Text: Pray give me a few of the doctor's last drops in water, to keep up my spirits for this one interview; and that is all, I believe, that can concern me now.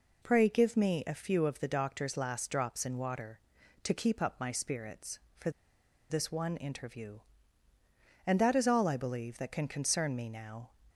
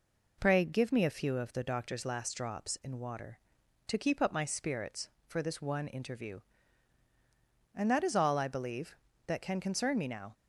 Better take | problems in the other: second | pauses between "for" and "this"; noticeable; at 5.4 s; 0.60 s long

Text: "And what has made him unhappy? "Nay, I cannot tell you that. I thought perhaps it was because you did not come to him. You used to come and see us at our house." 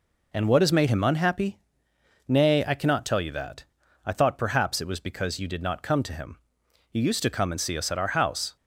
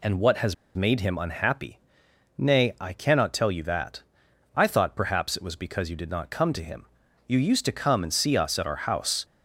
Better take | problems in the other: first | pauses between "has" and "made"; slight; at 0.5 s; 0.21 s long

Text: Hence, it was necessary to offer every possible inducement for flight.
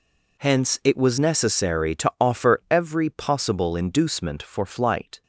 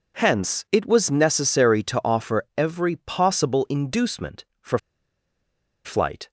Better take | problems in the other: first | pauses between "for" and "flight"; at 4.7 s; 1.0 s long

